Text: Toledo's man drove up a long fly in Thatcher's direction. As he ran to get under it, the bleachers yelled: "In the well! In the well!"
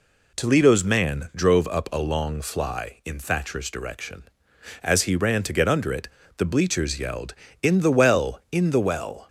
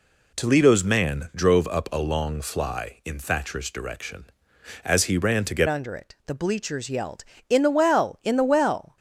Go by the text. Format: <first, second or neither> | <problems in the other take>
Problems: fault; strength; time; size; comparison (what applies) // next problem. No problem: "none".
first | changes voice at "under"; from 5.6 s on; 3.3 s long